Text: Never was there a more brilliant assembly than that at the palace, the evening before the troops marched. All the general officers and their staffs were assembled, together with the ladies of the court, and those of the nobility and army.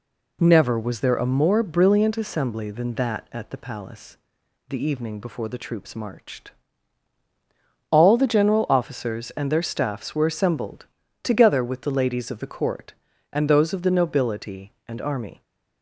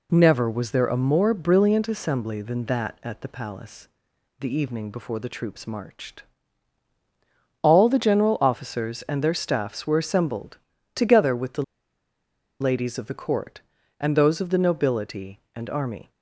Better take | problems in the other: first | pauses between "the" and "ladies"; noticeable; at 11.6 s; 0.97 s long

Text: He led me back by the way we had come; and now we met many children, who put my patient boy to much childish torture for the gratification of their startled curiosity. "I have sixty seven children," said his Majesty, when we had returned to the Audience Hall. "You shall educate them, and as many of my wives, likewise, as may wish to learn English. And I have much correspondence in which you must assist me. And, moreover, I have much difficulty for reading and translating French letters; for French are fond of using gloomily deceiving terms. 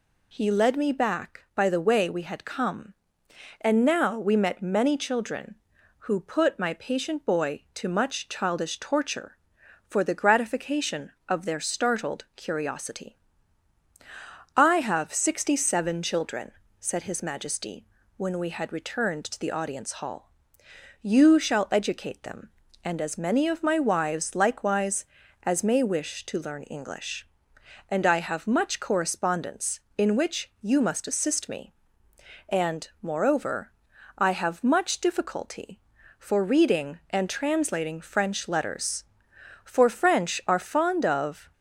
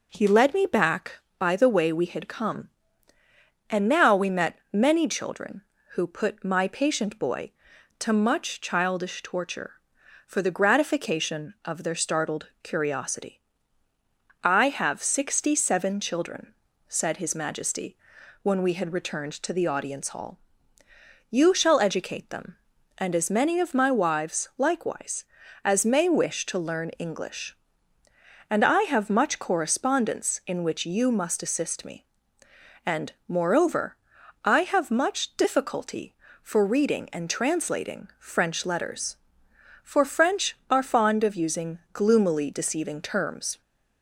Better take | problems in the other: second | stops before "using gloomily deceiving terms"; at 41.5 s

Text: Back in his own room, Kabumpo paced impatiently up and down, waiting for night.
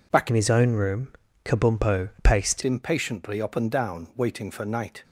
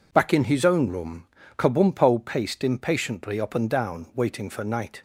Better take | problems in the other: second | changes voice from "in" to "paced"; from 0.2 to 2.6 s; 2.4 s long

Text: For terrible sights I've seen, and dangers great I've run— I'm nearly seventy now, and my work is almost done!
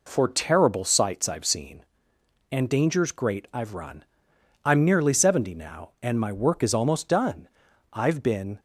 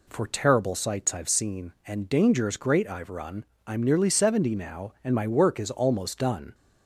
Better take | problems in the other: second | goes on to say "I've been"; noticeable; from 7.9 s on; 0.68 s long

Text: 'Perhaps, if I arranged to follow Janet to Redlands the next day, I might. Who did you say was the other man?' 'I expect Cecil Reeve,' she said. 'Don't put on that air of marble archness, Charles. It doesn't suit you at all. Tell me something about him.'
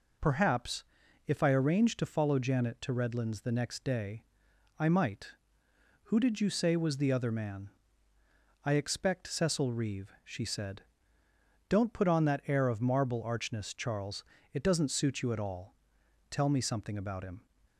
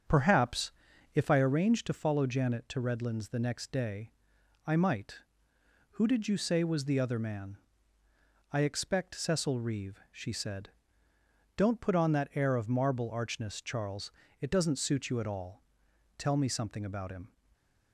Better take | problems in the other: first | starts louder than the rest; strong; until 1.5 s; 7.5 dB // stays silent after the last word; slight; from 17.2 s on; 0.7 s long

